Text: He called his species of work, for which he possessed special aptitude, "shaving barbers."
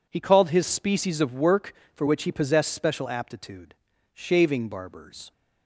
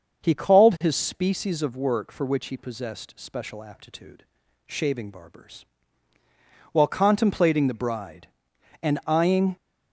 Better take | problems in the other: first | starts louder than the rest; until 1.2 s; 6.5 dB // goes on to say "While contemplating the bride and eyeing"; strong; from 6.7 s on; 2.8 s long

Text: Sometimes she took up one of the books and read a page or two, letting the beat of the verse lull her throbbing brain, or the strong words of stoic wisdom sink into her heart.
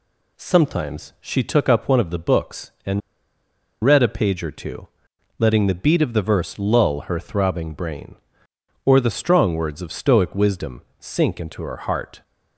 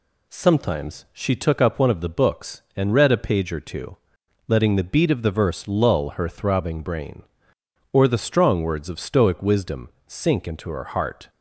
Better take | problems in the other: second | pauses between "and" and "read"; noticeable; at 3.0 s; 0.83 s long // pauses between "wisdom" and "sink"; slight; at 10.8 s; 0.18 s long; slight in the second

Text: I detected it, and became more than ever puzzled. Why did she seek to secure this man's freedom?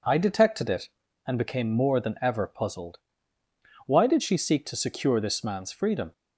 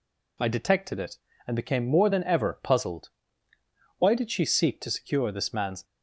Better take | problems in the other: first | stops before "freedom"; at 5.8 s

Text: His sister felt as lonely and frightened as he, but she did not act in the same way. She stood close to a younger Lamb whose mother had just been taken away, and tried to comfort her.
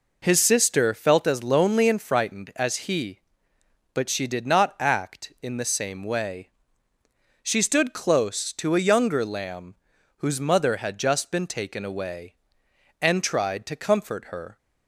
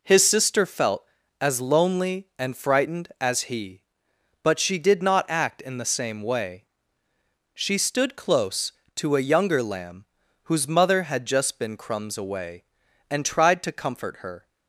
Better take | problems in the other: first | pauses between "Lamb" and "whose"; at 10.0 s; 0.40 s long; also in the first // says "crumbs" for "taken"; at 11.7 s

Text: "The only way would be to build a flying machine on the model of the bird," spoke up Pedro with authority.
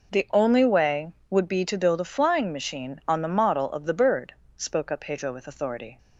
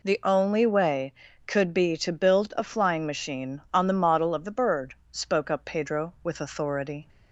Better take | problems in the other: first | says "could" for "would"; at 1.4 s

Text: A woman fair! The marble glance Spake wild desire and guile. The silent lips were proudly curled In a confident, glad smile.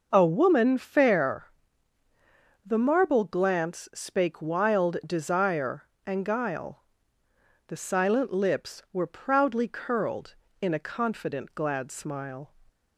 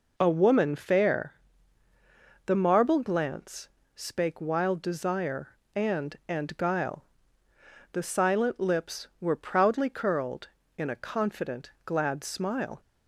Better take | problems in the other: first | pauses between "glance" and "Spake"; slight; at 3.6 s; 0.26 s long // says "and" twice; at 6.2 s

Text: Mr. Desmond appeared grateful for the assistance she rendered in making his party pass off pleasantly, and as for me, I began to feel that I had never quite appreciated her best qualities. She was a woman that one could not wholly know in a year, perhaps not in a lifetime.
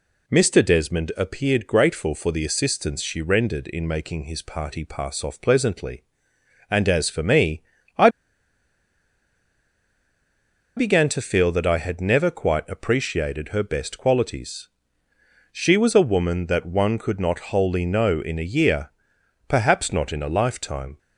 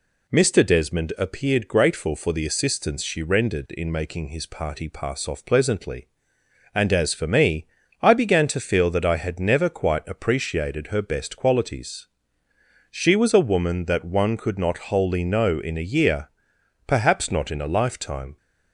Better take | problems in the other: second | pauses between "I" and "began"; strong; at 8.0 s; 2.6 s long

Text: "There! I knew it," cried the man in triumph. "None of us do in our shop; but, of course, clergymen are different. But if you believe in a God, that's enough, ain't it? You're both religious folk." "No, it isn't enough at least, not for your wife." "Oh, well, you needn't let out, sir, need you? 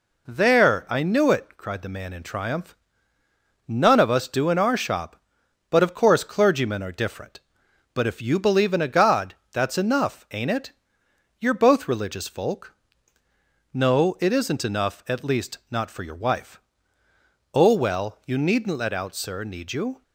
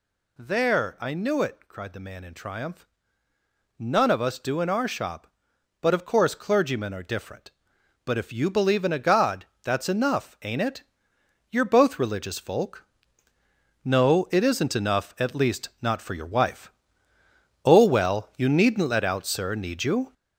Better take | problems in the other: first | gets louder; throughout; 6.5 dB

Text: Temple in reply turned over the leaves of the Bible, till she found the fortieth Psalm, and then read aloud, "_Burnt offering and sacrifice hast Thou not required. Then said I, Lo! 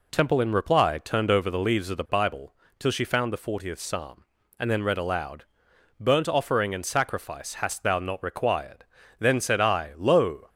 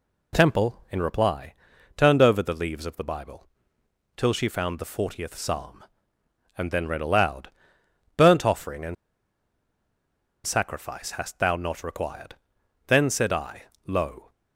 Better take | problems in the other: first | pauses between "reply" and "turned"; at 1.5 s; 0.42 s long // pauses between "and" and "sacrifice"; strong; at 8.9 s; 1.5 s long

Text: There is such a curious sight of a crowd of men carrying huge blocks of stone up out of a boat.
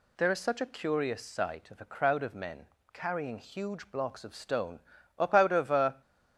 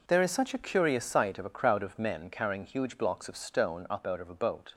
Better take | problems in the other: second | pauses between "men" and "carrying"; slight; at 2.6 s; 0.24 s long // pauses between "stone" and "up"; slight; at 4.8 s; 0.36 s long // stops before "boat"; at 6.0 s

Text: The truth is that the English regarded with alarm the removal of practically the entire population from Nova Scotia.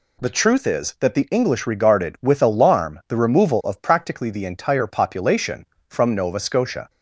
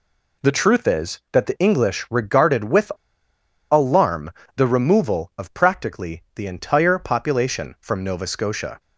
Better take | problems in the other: first | pauses between "with" and "alarm"; noticeable; at 2.9 s; 0.77 s long // pauses between "alarm" and "the"; slight; at 4.2 s; 0.26 s long

